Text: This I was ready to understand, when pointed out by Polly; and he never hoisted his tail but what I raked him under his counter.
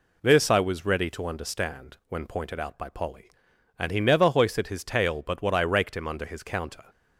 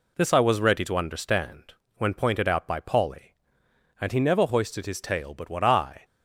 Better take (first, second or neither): first